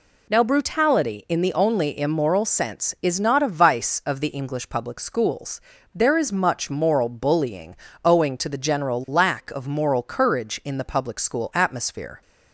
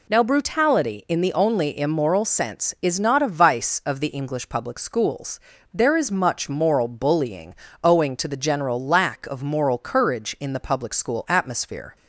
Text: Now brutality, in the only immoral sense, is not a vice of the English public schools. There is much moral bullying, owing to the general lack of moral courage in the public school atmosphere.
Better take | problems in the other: neither | none

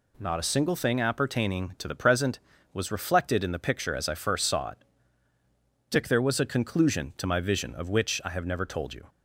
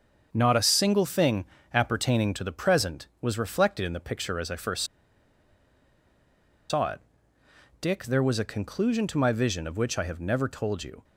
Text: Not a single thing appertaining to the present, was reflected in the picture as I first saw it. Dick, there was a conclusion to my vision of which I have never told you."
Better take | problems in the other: first | starts louder than the rest; until 1.3 s; 7 dB // pauses between "thing" and "appertaining"; slight; at 1.4 s; 0.28 s long // pauses between "first" and "saw"; strong; at 4.8 s; 1.8 s long

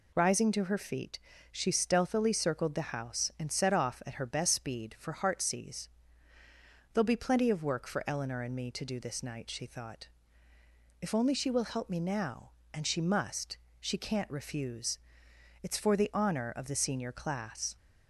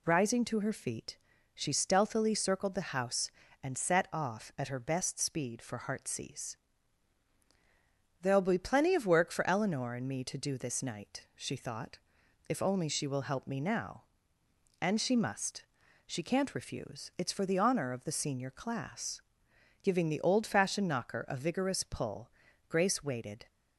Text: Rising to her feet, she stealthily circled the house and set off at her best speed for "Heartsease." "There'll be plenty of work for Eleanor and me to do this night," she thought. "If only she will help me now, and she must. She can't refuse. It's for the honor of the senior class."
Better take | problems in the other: first | goes on to say "Giving the old fashioned knocker a vigorous pull Grace waited"; strong; from 19.8 s on; 3.6 s long

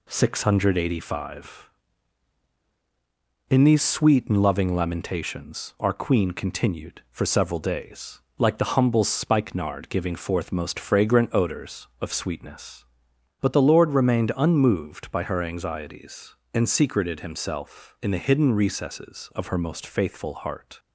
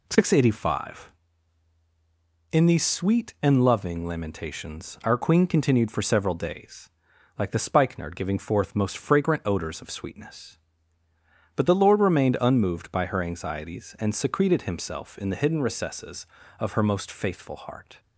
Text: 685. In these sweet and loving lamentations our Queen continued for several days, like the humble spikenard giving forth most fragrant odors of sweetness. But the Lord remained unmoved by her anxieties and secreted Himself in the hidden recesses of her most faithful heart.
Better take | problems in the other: first | skips "humble"; at 7.5 s

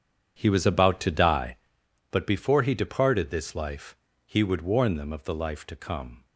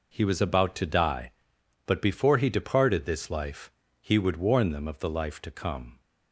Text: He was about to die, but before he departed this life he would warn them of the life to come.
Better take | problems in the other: second | starts louder than the rest; strong; until 1.7 s; 8.5 dB // pauses between "life" and "he"; slight; at 3.9 s; 0.26 s long; slight in the second

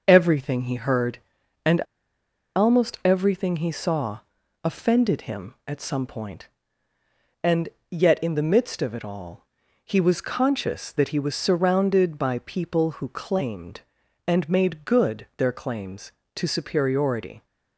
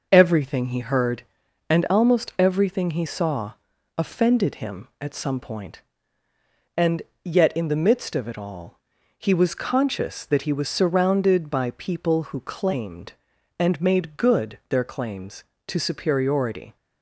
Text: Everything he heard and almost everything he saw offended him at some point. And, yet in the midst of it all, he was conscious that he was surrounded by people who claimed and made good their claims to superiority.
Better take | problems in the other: second | pauses between "and" and "almost"; noticeable; at 1.7 s; 0.76 s long // pauses between "saw" and "offended"; noticeable; at 4.1 s; 0.46 s long; noticeable in the second

